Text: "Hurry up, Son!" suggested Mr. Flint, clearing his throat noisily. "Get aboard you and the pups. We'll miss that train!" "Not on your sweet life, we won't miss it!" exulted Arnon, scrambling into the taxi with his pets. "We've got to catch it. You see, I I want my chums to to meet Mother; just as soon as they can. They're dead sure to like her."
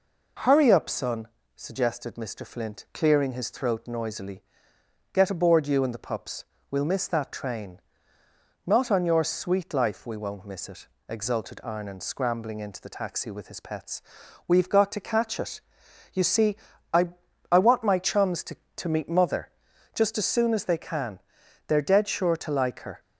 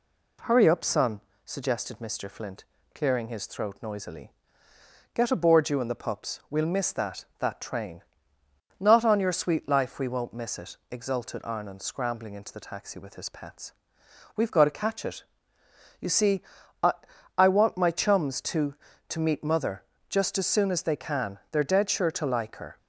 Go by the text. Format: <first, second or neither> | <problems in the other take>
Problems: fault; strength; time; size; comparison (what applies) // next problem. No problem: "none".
first | says "that" twice; at 7.3 s // pauses between "I" and "I"; at 16.9 s; 0.44 s long; also in the first